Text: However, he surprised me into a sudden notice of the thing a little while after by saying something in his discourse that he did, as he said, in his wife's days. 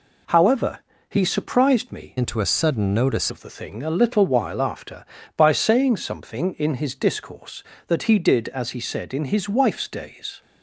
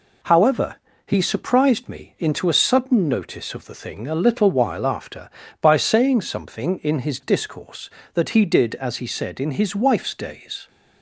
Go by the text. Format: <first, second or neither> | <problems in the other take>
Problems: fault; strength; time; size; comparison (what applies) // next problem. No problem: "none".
second | changes voice from "into" to "notice"; from 2.1 to 3.3 s; 1.2 s long